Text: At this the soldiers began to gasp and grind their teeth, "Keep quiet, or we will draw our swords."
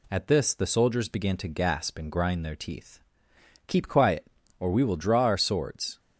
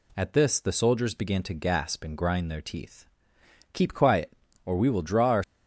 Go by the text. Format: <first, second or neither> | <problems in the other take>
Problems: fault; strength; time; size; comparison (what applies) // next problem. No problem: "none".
first | stops before "swords"; at 5.4 s